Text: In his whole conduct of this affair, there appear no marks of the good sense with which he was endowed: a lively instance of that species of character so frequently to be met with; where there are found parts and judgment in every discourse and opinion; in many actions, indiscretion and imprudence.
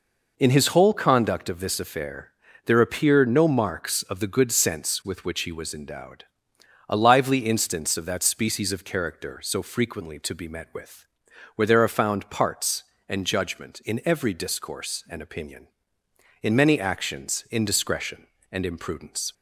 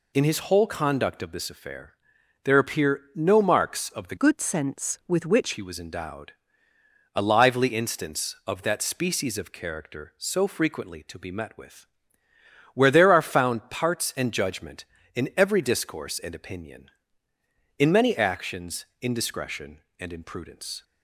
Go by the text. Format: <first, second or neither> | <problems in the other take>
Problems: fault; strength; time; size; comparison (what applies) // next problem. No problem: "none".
first | changes voice from "good" to "which"; from 4.1 to 5.5 s; 1.4 s long